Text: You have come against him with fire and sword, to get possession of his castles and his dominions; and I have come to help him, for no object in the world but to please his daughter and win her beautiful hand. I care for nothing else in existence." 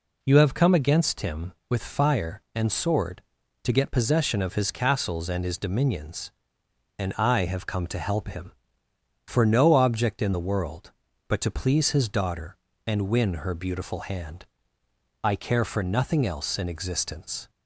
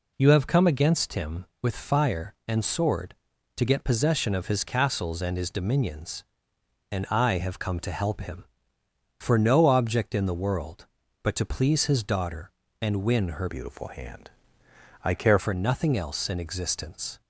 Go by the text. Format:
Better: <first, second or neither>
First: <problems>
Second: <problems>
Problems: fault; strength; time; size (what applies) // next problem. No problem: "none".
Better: first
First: none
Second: changes voice from "beautiful" to "care"; from 13.4 to 15.3 s; 1.9 s long